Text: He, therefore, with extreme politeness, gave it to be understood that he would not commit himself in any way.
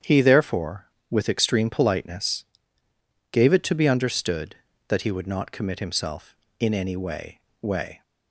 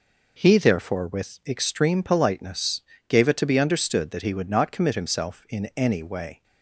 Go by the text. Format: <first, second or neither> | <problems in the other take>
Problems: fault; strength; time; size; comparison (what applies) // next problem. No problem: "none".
second | starts louder than the rest; strong; until 1.2 s; 8.5 dB // says "way" twice; at 7.6 s